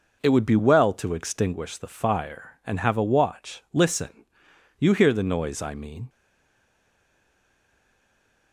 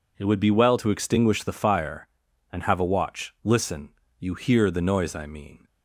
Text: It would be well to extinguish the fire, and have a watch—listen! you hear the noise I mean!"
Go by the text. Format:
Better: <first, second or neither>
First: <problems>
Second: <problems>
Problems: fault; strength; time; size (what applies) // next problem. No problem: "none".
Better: second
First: stays silent after the last word; from 6.0 s on; 2.5 s long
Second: none